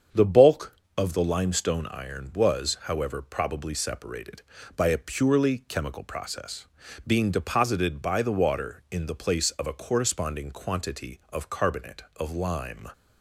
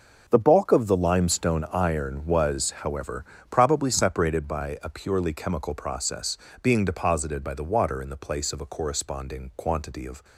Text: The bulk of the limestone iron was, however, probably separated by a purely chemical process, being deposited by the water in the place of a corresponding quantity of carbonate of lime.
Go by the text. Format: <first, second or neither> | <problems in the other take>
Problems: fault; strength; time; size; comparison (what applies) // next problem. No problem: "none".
first | starts louder than the rest; until 1.2 s; 7 dB; strong in the first // stops before "carbonate of lime"; at 10.2 s